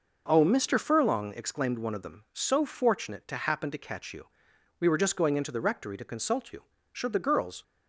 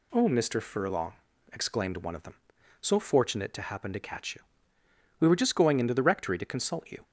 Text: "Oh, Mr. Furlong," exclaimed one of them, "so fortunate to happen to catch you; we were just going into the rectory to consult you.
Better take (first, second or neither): second